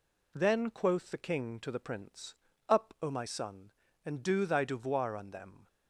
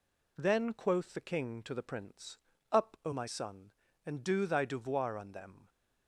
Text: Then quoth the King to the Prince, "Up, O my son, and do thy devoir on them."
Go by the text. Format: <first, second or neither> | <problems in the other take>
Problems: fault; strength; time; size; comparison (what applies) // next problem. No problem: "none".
neither | none